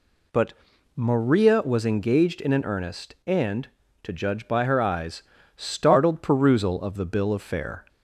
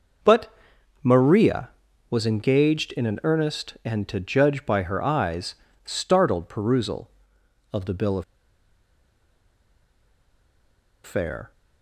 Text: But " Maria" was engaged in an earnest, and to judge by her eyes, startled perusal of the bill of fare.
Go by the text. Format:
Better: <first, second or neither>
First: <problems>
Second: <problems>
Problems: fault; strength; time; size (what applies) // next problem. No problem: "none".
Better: first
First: none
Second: pauses between "of" and "fare"; strong; at 8.2 s; 2.8 s long